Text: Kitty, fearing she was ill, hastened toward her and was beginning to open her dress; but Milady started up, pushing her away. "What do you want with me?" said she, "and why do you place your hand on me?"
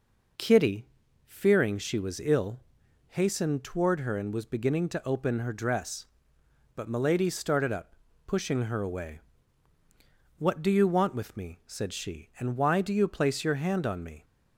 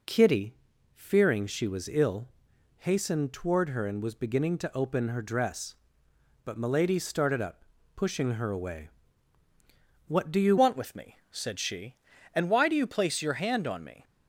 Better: first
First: none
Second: changes voice at "want"; from 10.5 s on; 3.5 s long

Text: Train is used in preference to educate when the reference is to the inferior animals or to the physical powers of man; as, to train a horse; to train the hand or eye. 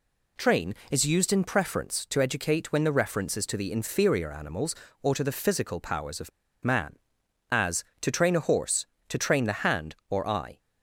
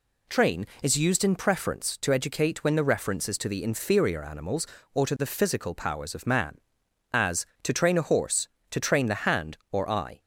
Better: second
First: pauses between "of" and "man"; slight; at 6.3 s; 0.33 s long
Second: none

